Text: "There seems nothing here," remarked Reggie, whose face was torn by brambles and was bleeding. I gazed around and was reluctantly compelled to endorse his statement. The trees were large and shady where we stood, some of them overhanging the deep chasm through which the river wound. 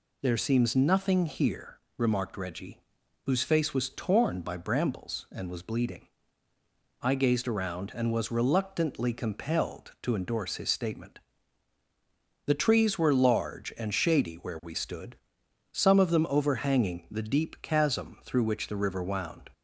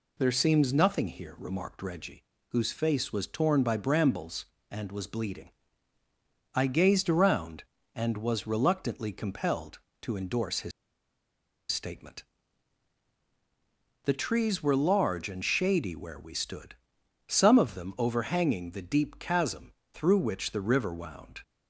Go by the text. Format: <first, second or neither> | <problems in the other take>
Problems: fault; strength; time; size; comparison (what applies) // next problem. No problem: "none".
first | pauses between "his" and "statement"; at 10.7 s; 1.0 s long // pauses between "chasm" and "through"; slight; at 19.7 s; 0.20 s long